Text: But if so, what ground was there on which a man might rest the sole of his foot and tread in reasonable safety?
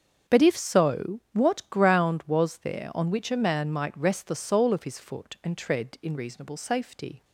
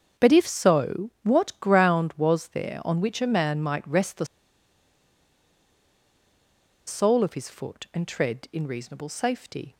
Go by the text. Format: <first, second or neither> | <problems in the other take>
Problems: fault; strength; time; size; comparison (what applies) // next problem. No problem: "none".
first | starts louder than the rest; until 1.3 s; 6.5 dB; also in the first // pauses between "the" and "sole"; strong; at 4.2 s; 2.6 s long